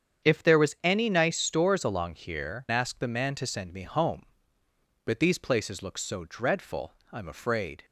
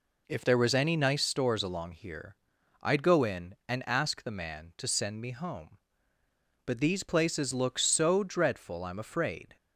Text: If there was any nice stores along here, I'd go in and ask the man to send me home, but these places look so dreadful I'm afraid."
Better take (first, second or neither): second